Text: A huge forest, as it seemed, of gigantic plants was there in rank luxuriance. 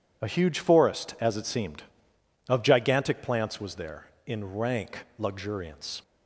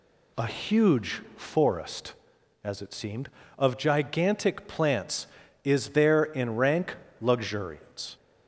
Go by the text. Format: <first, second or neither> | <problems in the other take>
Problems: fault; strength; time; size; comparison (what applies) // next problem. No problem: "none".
first | says "is" for "was"; at 5.6 s // pauses between "rank" and "luxuriance"; slight; at 6.9 s; 0.24 s long